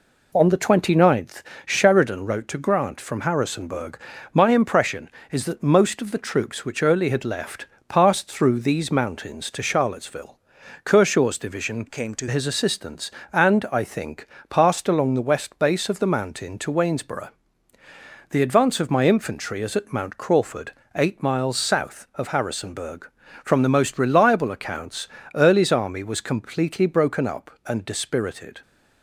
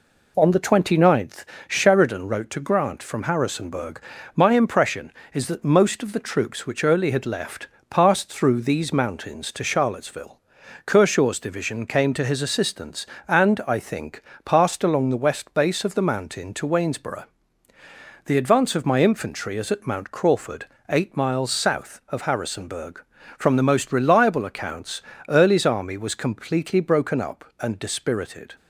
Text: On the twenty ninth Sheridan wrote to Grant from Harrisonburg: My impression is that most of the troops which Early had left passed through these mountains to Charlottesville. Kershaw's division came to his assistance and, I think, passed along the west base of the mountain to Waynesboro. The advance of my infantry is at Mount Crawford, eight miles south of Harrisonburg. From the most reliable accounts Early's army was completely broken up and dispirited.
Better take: second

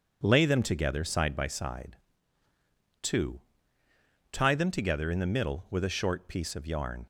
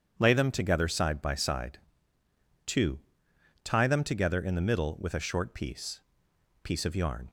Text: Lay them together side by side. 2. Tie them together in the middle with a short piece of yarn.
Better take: first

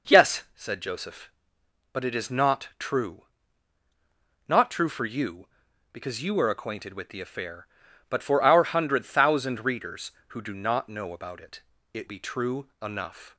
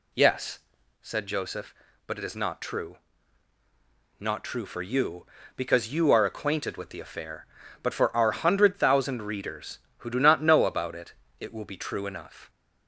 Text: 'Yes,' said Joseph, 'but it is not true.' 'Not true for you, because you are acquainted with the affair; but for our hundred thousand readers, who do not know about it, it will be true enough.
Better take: second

